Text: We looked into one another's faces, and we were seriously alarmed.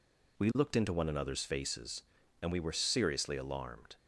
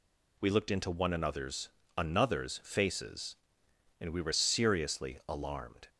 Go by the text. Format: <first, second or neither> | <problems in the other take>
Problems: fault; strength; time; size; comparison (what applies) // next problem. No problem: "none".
first | says "another's" twice; at 1.9 s